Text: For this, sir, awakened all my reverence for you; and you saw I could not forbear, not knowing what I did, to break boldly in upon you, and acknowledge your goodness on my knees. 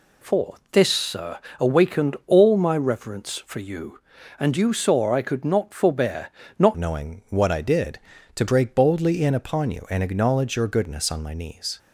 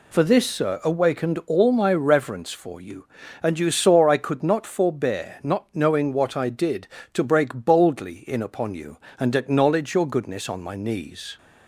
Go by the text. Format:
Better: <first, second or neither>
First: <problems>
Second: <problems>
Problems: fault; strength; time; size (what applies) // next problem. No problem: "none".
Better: second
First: pauses between "For" and "this"; slight; at 0.5 s; 0.16 s long // changes voice at "knowing"; from 6.7 s on; 5.0 s long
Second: none